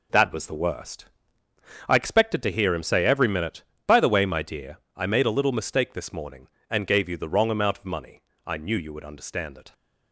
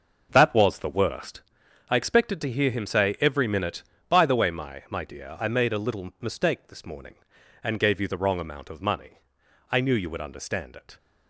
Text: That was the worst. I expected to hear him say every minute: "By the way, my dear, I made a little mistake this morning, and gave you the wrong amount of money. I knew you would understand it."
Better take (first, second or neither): first